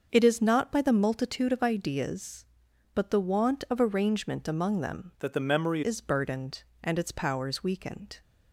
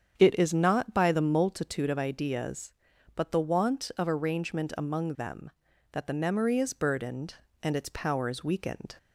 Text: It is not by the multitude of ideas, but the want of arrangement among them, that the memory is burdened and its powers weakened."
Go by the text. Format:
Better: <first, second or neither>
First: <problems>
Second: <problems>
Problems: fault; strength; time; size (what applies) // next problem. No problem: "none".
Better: second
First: starts louder than the rest; until 1.1 s; 6.5 dB // changes voice from "that" to "memory"; from 5.1 to 5.8 s; 0.7 s long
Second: starts louder than the rest; strong; until 1.1 s; 8 dB